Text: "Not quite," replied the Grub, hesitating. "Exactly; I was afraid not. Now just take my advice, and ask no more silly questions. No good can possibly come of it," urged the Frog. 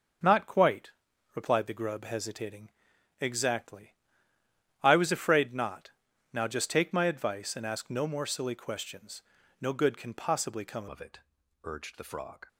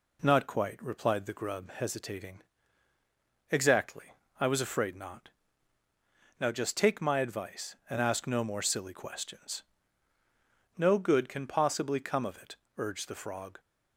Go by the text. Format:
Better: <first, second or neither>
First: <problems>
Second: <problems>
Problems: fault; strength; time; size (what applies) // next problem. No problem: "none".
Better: second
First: starts louder than the rest; until 1.6 s; 6.5 dB // changes voice at "of"; from 10.8 s on; 1.6 s long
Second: none